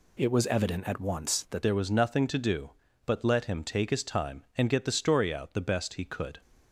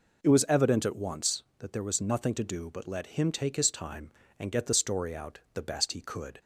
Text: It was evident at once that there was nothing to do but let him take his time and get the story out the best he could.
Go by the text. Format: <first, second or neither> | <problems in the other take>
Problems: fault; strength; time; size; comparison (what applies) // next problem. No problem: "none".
second | changes voice at "there"; from 1.6 s on; 4.8 s long